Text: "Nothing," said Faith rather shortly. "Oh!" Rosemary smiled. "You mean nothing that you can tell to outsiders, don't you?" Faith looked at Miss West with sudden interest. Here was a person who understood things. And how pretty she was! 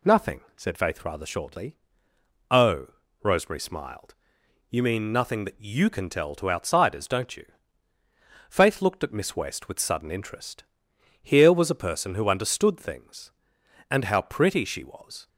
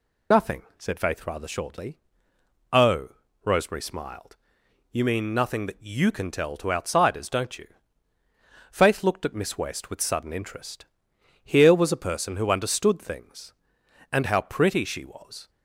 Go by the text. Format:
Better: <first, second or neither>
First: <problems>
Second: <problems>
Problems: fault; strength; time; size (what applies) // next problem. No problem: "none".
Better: first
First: none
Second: loses the start of "Nothing"; at 0.3 s; 55 ms